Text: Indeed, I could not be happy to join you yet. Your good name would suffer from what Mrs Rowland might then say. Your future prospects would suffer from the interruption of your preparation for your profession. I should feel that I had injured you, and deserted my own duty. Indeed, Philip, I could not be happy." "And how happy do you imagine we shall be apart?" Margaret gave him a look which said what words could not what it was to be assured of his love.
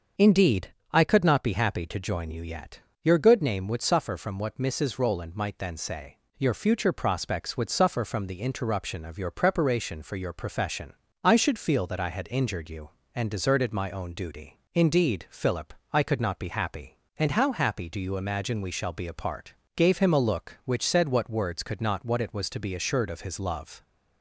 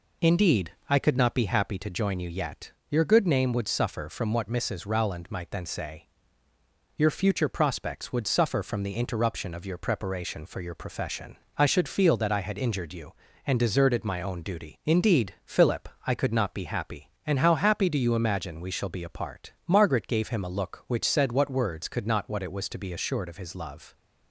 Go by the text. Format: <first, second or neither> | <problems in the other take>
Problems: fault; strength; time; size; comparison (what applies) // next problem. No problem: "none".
second | starts louder than the rest; until 1.3 s; 6.5 dB // skips "Margaret"; at 19.6 s